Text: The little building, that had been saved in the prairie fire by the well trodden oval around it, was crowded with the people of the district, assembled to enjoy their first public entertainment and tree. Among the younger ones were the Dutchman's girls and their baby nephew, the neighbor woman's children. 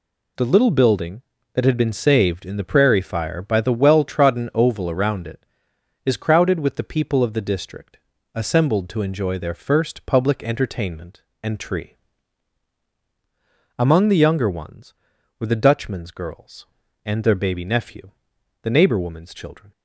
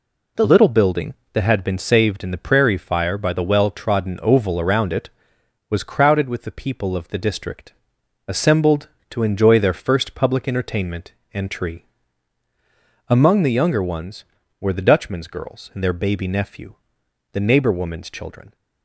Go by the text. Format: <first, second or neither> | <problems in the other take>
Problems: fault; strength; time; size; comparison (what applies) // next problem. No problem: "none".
second | says "is" for "was"; at 6.0 s